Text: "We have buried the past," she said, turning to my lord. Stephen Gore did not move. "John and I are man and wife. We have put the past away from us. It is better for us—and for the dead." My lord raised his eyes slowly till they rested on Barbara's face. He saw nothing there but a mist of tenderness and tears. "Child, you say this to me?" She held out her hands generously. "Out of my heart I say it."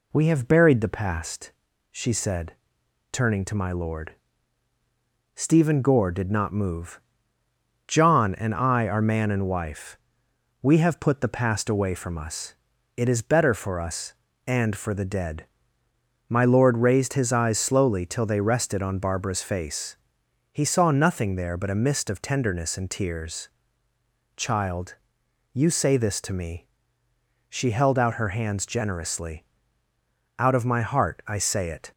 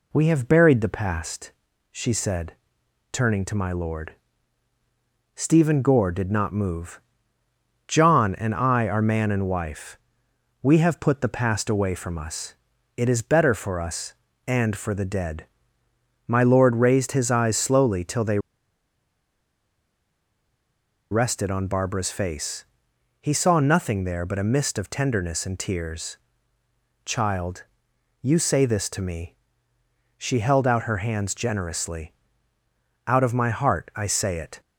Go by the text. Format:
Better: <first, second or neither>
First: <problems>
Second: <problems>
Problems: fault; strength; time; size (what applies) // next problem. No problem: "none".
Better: first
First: none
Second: pauses between "they" and "rested"; strong; at 18.3 s; 2.7 s long